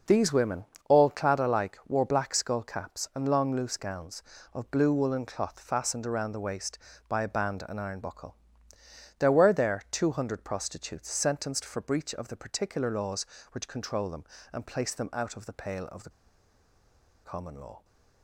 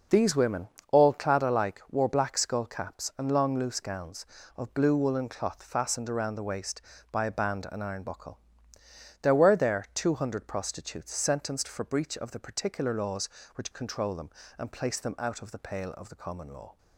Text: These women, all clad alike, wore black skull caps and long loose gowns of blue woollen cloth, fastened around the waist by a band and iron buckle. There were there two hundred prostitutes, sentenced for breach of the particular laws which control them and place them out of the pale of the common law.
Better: second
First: pauses between "the" and "common"; at 16.0 s; 1.1 s long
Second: none

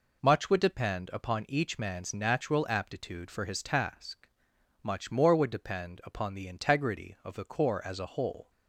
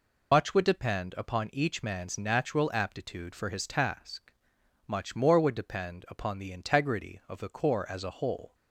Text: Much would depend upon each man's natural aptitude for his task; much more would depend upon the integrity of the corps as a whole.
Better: first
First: none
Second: loses the start of "Much"; at 0.3 s; 55 ms

